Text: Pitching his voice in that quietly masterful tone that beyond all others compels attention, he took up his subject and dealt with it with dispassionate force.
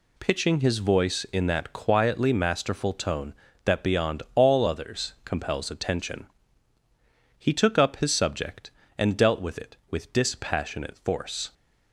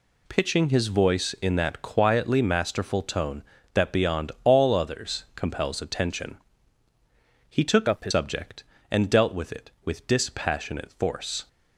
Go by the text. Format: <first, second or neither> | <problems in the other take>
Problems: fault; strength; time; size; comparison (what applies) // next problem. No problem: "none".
first | changes voice from "up" to "his"; from 7.8 to 8.1 s; 0.3 s long